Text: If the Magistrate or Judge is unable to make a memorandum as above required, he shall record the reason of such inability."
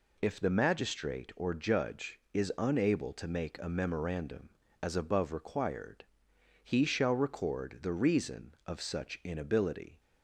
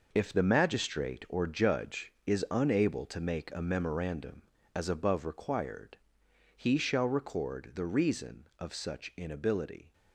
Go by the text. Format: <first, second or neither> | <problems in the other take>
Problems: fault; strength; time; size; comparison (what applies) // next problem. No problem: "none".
first | gets quieter; strong; throughout; 10 dB